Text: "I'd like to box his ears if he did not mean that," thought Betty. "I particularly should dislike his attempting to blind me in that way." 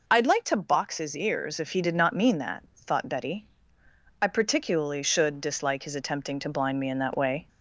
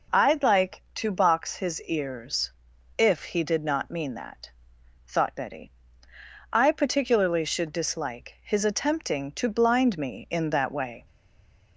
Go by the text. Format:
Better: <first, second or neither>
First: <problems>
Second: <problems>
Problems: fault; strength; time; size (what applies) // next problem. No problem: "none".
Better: first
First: none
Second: pauses between "ears" and "if"; noticeable; at 2.5 s; 0.46 s long // stays silent after the last word; slight; from 11.0 s on; 0.7 s long